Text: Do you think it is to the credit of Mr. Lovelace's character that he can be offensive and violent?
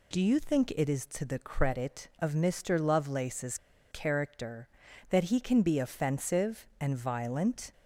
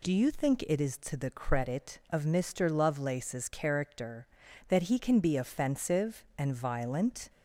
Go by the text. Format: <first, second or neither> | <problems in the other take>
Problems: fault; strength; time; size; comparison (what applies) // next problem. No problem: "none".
second | pauses between "Lovelace's" and "character"; slight; at 3.5 s; 0.34 s long